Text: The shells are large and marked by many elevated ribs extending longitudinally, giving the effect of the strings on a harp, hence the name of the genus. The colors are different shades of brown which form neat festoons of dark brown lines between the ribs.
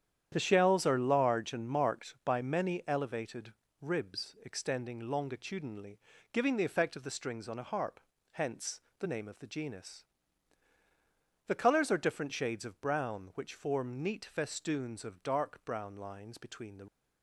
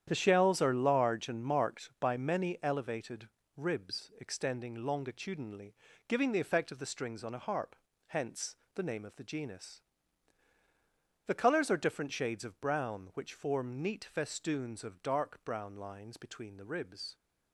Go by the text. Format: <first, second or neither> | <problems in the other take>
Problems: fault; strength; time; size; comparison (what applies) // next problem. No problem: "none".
second | starts louder than the rest; strong; until 1.3 s; 9.5 dB; strong in the second // pauses between "elevated" and "ribs"; slight; at 3.5 s; 0.30 s long; slight in the second // pauses between "hence" and "the"; slight; at 8.8 s; 0.16 s long; slight in the second // stops before "ribs"; at 16.8 s